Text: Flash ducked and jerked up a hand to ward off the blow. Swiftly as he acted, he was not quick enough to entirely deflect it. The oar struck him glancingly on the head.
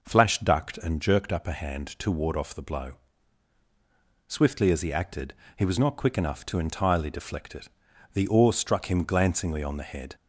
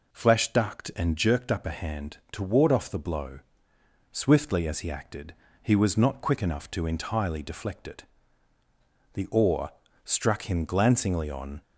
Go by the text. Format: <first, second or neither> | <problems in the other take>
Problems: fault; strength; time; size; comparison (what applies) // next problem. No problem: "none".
first | pauses between "oar" and "struck"; slight; at 9.7 s; 0.32 s long // stops before "the head"; at 11.6 s